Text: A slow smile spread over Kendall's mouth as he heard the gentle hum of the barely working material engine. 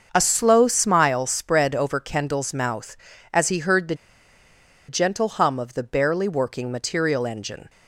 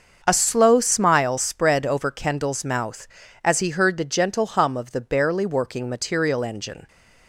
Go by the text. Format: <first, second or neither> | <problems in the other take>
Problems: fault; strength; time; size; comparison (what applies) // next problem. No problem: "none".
second | starts louder than the rest; until 1.1 s; 6.5 dB; also in the second // pauses between "the" and "gentle"; noticeable; at 3.9 s; 0.94 s long